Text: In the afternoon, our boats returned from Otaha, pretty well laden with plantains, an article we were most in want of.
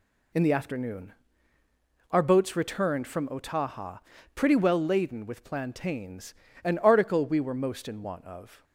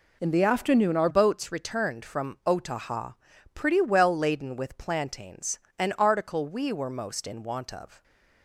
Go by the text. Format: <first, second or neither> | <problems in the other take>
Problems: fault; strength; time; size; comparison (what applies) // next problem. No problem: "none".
first | changes voice at "boats"; from 1.0 s on; 7.0 s long